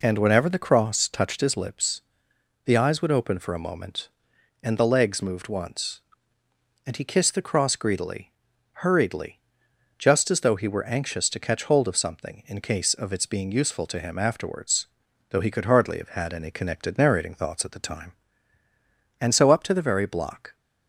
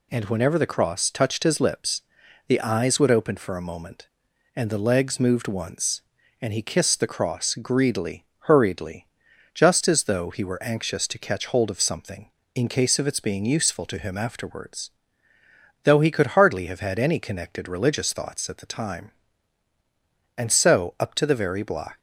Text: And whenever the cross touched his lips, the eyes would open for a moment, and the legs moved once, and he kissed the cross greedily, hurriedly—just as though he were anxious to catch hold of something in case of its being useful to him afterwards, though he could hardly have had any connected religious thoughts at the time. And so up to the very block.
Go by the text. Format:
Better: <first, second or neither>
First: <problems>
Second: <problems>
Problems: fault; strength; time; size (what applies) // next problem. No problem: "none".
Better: second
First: says "narrating" for "religious"; at 16.9 s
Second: none